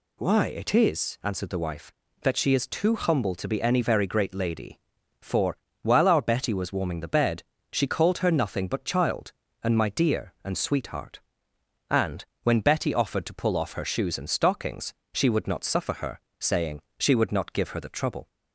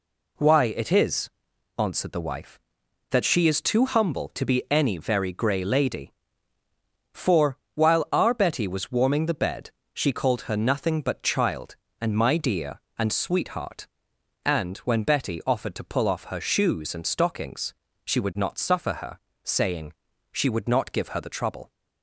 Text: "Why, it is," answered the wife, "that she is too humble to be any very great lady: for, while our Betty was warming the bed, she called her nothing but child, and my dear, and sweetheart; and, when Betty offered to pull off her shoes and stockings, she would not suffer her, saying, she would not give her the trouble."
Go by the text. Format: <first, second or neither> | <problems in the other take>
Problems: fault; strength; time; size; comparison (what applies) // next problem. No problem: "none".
first | says "grey" for "great"; at 5.3 s